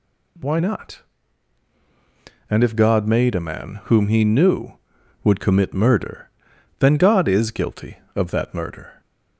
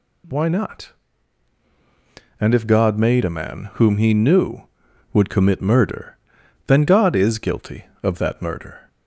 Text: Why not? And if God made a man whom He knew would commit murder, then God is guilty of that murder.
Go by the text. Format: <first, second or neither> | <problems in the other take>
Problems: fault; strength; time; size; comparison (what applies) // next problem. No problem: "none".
neither | none